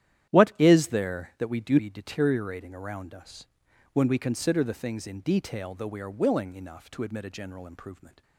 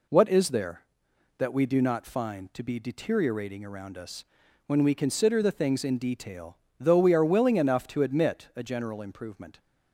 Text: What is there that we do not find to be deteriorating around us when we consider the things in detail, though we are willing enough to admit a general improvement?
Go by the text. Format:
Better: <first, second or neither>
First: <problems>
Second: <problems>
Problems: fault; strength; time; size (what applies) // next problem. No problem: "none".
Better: second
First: starts louder than the rest; strong; until 1.4 s; 11 dB // skips "not find to"; at 1.7 s // pauses between "us" and "when"; noticeable; at 3.4 s; 0.48 s long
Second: pauses between "us" and "when"; at 4.2 s; 0.44 s long